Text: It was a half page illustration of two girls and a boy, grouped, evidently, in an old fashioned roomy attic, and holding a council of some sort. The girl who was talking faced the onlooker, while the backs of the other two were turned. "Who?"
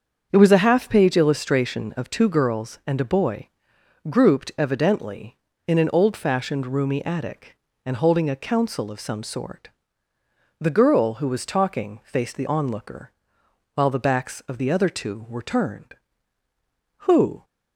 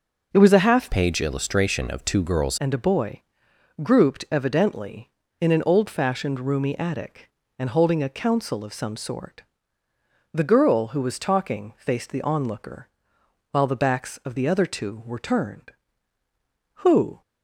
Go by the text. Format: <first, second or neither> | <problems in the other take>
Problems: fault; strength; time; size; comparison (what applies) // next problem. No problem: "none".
first | starts louder than the rest; until 1.3 s; 6 dB; also in the first // changes voice from "page" to "girls"; from 0.8 to 2.5 s; 1.7 s long